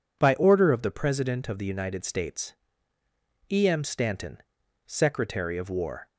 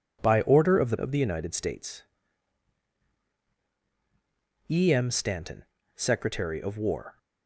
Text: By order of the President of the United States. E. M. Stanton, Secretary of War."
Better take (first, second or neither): first